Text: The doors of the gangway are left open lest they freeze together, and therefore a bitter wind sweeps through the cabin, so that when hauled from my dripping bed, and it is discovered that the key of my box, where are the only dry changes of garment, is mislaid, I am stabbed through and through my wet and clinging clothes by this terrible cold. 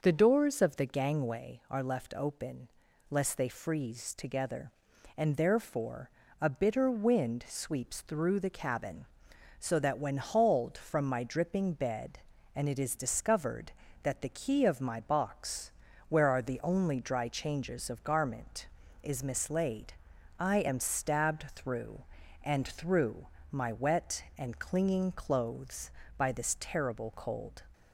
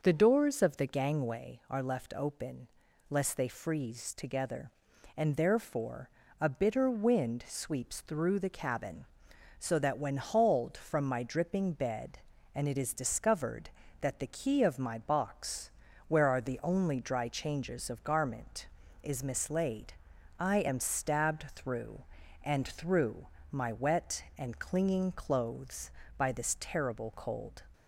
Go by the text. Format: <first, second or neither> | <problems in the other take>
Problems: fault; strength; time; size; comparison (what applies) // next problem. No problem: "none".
neither | pauses between "open" and "lest"; the same in both // pauses between "therefore" and "a"; slight; the same in both // pauses between "through" and "my"; slight; the same in both